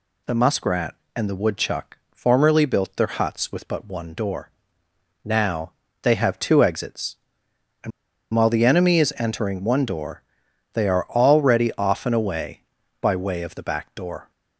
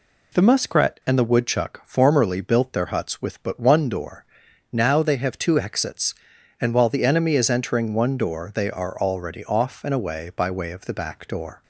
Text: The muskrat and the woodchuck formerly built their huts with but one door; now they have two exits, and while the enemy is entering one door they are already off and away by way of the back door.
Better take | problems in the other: second | pauses between "now" and "they"; slight; at 5.7 s; 0.28 s long // pauses between "and" and "while"; at 7.9 s; 0.43 s long // pauses between "door" and "they"; noticeable; at 10.2 s; 0.50 s long

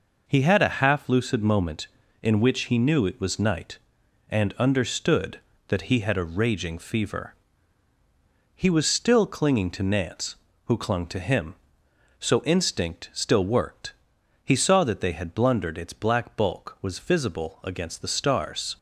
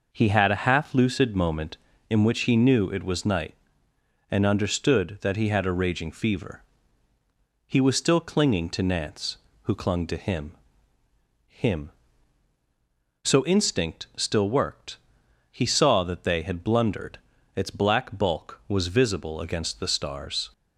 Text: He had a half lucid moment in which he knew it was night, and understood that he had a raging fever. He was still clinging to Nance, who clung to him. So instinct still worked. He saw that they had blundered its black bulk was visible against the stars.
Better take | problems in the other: first | says "him" twice; at 11.4 s // pauses between "blundered" and "its"; slight; at 17.1 s; 0.36 s long

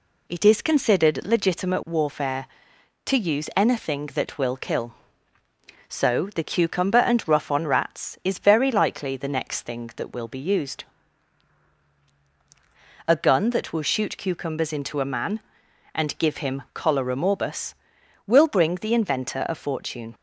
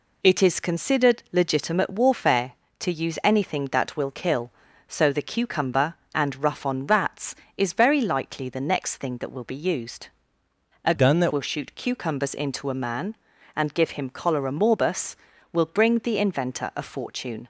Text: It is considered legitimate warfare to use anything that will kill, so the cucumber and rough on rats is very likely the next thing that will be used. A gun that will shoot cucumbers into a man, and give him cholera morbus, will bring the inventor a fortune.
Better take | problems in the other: first | changes voice from "gun" to "that"; from 10.9 to 11.3 s; 0.4 s long

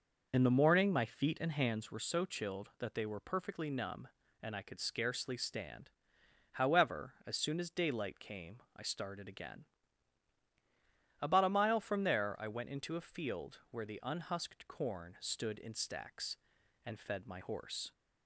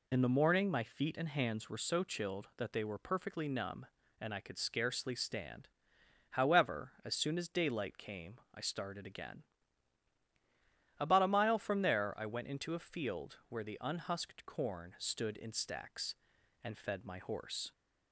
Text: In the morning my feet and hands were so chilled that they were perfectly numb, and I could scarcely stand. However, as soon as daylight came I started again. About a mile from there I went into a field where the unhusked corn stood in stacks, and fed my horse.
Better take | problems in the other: second | starts louder than the rest; noticeable; until 1.9 s; 6 dB // pauses between "came" and "I"; slight; at 8.5 s; 0.18 s long; slight in the second

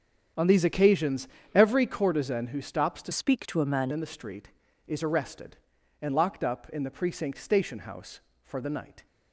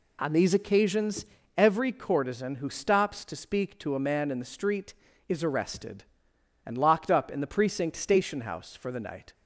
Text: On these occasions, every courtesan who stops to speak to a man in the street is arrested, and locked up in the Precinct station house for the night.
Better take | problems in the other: second | starts louder than the rest; strong; until 1.6 s; 8 dB // changes voice from "speak" to "man"; from 3.1 to 3.9 s; 0.8 s long

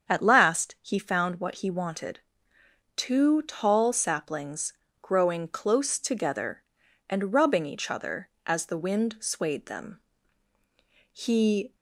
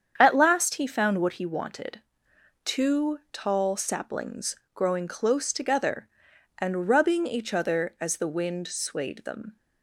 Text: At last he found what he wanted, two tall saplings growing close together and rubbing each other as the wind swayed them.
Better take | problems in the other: second | starts louder than the rest; strong; until 1.1 s; 7 dB; strong in the second // pauses between "saplings" and "growing"; slight; at 4.7 s; 0.28 s long; slight in the second // goes on to say "He"; noticeable; from 11.1 s on; 0.62 s long

